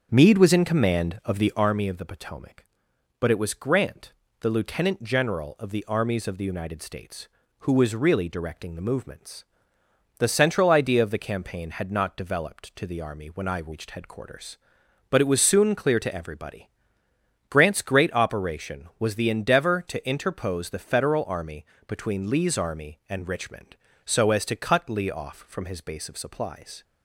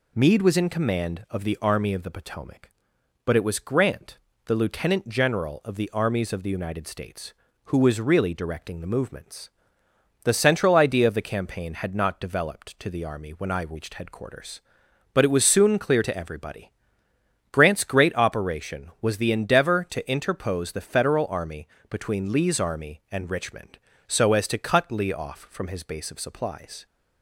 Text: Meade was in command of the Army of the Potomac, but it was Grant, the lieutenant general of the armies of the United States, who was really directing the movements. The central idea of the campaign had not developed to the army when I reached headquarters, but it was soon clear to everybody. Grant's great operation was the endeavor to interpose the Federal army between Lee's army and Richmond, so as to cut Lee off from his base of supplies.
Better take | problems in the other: second | starts louder than the rest; until 1.7 s; 7 dB // pauses between "army" and "between"; slight; at 21.6 s; 0.22 s long; slight in the second

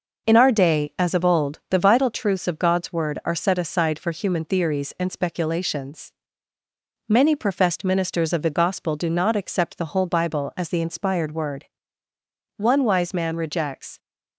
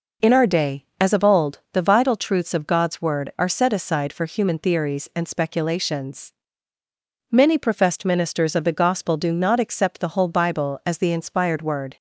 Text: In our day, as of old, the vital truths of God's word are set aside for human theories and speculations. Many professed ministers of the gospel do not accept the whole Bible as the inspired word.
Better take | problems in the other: second | goes on to say "One wise man rejects"; from 12.5 s on; 1.4 s long

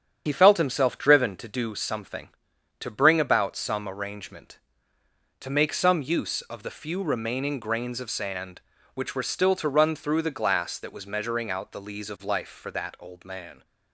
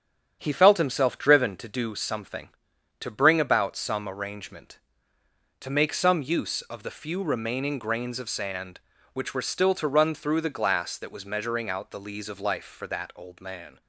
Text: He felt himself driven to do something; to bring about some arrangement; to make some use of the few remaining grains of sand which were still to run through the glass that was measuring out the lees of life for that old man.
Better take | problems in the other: second | loses the start of "He"; at 0.2 s; 45 ms // starts louder than the rest; strong; until 1.2 s; 8 dB; strong in the second

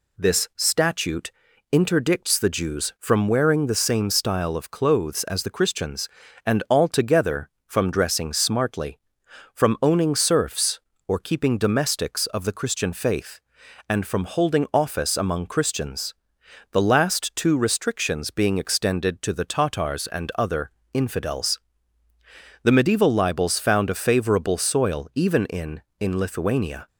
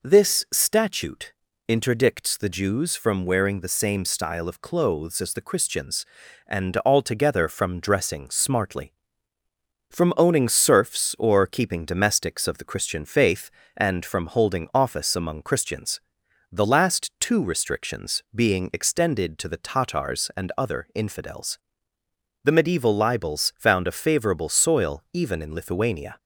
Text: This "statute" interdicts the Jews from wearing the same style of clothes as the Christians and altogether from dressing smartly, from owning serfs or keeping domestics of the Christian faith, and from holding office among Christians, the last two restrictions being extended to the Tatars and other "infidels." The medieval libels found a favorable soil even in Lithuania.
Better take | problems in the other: second | pauses between "statute" and "interdicts"; at 1.3 s; 0.40 s long; slight in the second // pauses between "other" and "infidels"; slight; at 20.7 s; 0.24 s long // says "in" twice; at 25.9 s

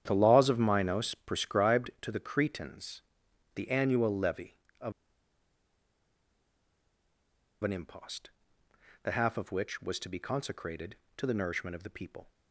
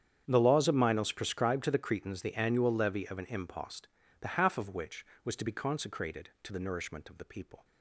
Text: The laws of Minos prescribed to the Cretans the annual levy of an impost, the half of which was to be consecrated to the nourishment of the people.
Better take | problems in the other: second | starts louder than the rest; strong; until 1.0 s; 9.5 dB; strong in the second // pauses between "Cretans" and "the"; noticeable; at 3.0 s; 0.54 s long // pauses between "of" and "an"; strong; at 4.9 s; 2.7 s long

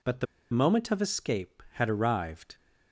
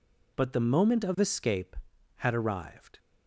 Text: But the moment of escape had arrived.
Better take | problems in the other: second | pauses between "the" and "moment"; slight; at 0.2 s; 0.25 s long

